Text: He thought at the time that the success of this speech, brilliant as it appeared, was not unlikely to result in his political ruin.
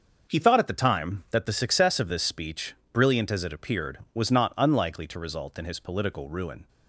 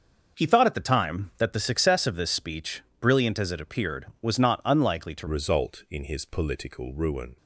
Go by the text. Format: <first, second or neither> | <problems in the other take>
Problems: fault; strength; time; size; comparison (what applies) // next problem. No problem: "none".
first | starts louder than the rest; until 1.4 s; 6.5 dB; also in the first // changes voice at "result"; from 5.2 s on; 2.1 s long